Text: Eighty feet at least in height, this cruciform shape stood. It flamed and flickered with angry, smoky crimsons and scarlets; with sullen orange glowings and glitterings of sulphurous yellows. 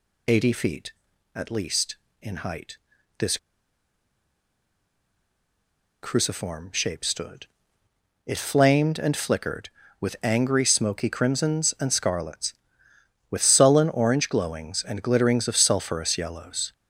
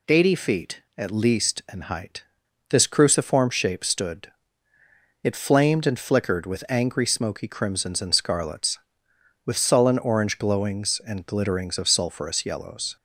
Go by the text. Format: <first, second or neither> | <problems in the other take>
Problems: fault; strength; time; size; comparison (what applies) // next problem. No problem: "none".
second | pauses between "this" and "cruciform"; strong; at 3.3 s; 2.6 s long